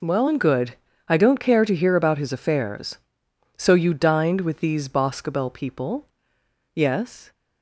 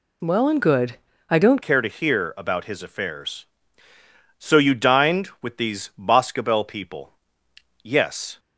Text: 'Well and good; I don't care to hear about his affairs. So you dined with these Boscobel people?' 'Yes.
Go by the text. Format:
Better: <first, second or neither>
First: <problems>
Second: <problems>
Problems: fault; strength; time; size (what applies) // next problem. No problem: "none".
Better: first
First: none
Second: changes voice at "care"; from 1.6 s on; 6.7 s long